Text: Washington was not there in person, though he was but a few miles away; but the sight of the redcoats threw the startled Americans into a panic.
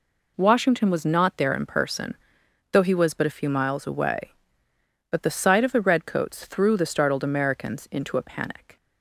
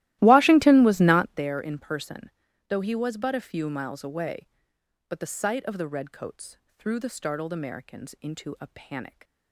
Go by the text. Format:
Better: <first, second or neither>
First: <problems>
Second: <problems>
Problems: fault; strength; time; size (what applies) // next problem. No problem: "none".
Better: first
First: none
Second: starts louder than the rest; strong; until 1.5 s; 16 dB // pauses between "redcoats" and "threw"; slight; at 6.5 s; 0.22 s long